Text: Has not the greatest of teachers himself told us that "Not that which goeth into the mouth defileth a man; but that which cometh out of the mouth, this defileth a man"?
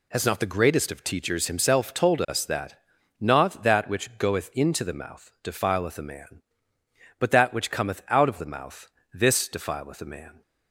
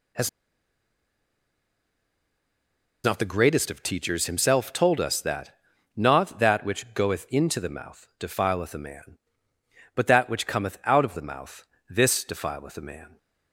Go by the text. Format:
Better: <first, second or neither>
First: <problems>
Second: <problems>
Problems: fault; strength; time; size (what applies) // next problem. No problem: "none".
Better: first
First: pauses between "that" and "Not"; at 2.7 s; 0.42 s long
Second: pauses between "Has" and "not"; strong; at 0.2 s; 2.7 s long // pauses between "that" and "Not"; at 5.5 s; 0.42 s long